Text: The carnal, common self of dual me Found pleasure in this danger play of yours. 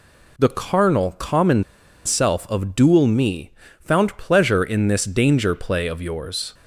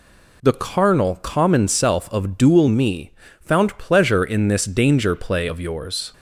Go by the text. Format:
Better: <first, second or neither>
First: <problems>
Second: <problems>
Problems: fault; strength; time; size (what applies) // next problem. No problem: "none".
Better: second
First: pauses between "common" and "self"; at 1.6 s; 0.43 s long // pauses between "me" and "Found"; slight; at 3.5 s; 0.30 s long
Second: pauses between "me" and "Found"; slight; at 3.1 s; 0.30 s long